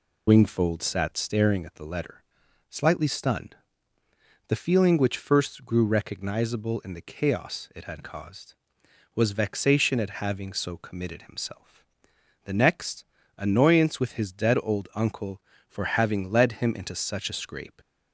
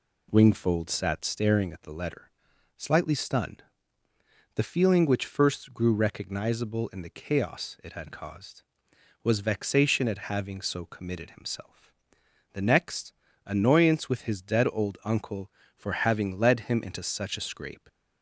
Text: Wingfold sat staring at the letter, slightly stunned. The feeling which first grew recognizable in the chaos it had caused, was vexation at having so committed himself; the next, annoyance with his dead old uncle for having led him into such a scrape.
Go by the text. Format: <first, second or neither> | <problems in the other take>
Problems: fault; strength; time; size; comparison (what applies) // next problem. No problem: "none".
second | loses the start of "Wingfold"; at 0.2 s; 65 ms